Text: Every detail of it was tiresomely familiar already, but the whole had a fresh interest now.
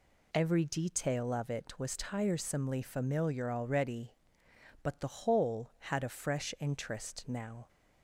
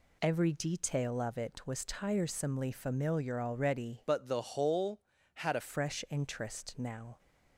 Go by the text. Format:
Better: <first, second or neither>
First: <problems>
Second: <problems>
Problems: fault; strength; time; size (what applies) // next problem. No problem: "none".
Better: first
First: none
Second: changes voice from "but" to "a"; from 4.0 to 5.6 s; 1.6 s long